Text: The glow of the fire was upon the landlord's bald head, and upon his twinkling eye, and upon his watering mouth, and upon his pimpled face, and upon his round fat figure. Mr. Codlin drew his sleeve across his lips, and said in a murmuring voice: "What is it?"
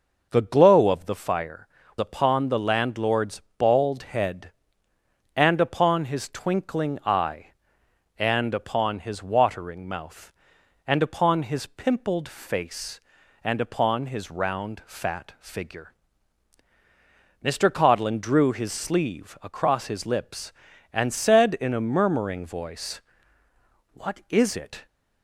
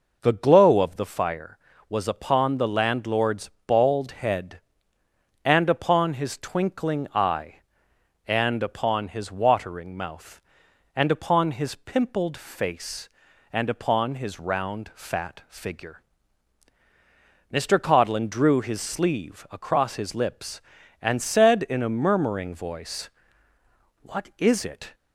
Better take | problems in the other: second | skips "was"; at 1.8 s // pauses between "landlord's" and "bald"; slight; at 3.4 s; 0.16 s long; slight in the second

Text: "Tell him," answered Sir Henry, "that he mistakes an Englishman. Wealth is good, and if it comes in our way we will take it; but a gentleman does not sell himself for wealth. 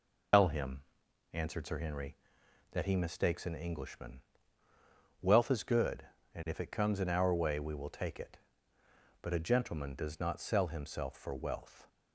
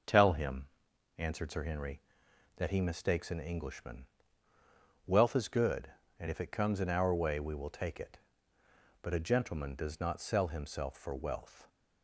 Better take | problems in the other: second | loses the start of "Tell"; at 0.3 s; 120 ms

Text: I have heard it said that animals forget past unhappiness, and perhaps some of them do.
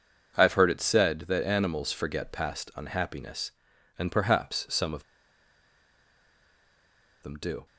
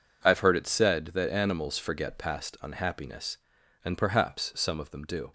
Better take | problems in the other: second | pauses between "of" and "them"; strong; at 5.0 s; 2.1 s long

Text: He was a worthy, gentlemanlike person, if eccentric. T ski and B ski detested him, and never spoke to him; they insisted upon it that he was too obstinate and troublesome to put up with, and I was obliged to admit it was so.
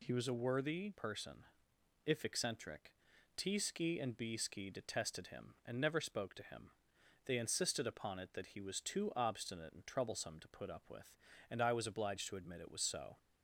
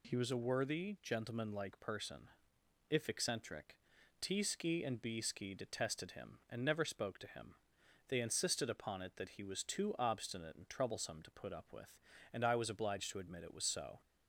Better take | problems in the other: second | skips "gentlemanlike"; at 0.9 s

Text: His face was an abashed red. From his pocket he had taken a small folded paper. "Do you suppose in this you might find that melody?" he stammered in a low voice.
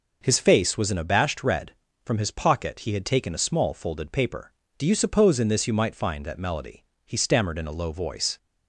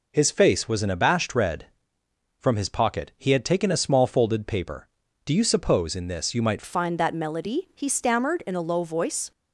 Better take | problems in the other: first | changes voice at "find"; from 6.6 s on; 2.7 s long

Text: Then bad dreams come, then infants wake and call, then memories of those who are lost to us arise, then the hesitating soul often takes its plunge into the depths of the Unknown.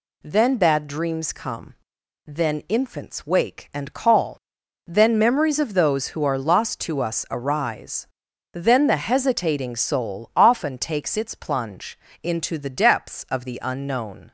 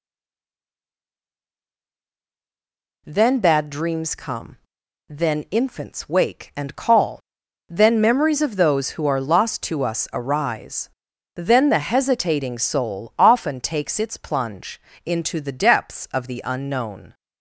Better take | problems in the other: first | stays silent before the first word; strong; until 3.0 s; 3.0 s long // pauses between "plunge" and "into"; slight; at 14.7 s; 0.24 s long; slight in the first

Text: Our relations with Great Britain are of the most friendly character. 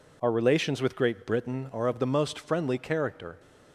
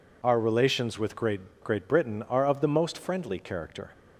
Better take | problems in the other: first | says "Great" twice; at 1.6 s

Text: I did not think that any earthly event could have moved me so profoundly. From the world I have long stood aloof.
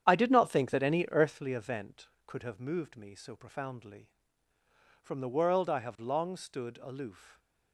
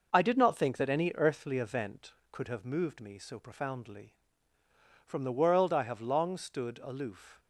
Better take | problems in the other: second | starts louder than the rest; strong; until 1.5 s; 9 dB

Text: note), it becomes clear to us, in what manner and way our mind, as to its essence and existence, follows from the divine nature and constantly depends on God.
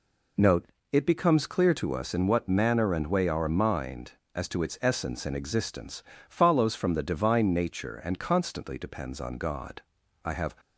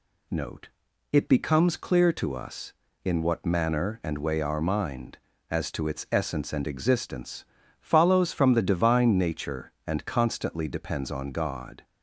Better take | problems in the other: second | goes on to say "I have"; slight; from 10.2 s on; 0.28 s long

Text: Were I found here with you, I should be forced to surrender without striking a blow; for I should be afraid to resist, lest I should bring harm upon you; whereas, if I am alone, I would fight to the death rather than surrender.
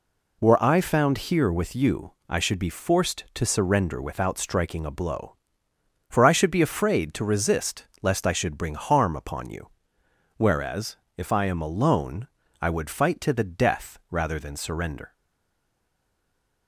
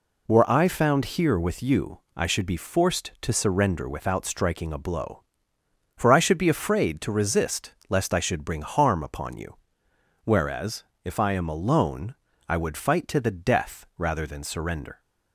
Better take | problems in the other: second | stays silent after the last word; noticeable; from 15.1 s on; 1.5 s long

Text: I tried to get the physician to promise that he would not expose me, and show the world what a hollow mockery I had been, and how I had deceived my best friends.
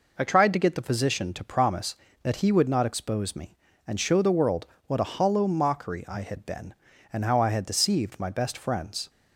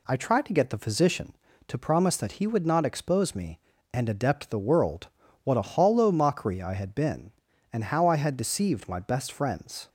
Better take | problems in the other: first | says "adept" for "show"; at 4.0 s // pauses between "world" and "what"; at 5.0 s; 0.38 s long; slight in the first

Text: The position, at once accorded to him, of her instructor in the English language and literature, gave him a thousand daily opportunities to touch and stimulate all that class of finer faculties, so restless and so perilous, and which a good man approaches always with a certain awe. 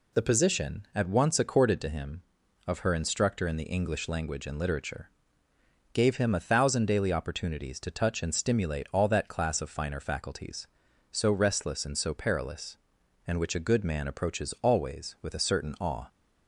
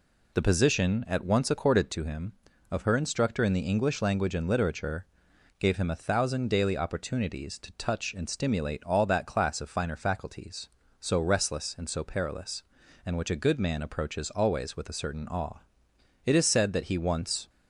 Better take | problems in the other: first | goes on to say "It is said that he once"; noticeable; from 16.2 s on; 1.2 s long

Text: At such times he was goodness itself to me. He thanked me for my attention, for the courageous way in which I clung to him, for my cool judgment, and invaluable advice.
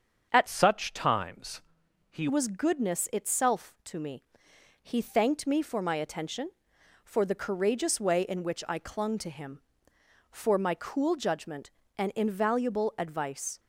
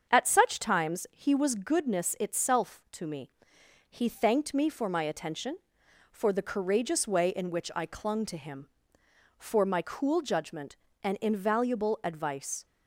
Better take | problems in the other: second | starts louder than the rest; until 1.3 s; 7 dB; strong in the second // changes voice from "such" to "he"; from 0.4 to 2.2 s; 1.8 s long // pauses between "times" and "he"; noticeable; at 1.6 s; 0.48 s long

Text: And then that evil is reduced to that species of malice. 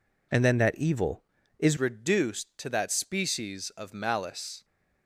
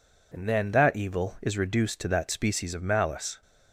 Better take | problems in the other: second | changes voice at "reduced"; from 1.7 s on; 2.9 s long

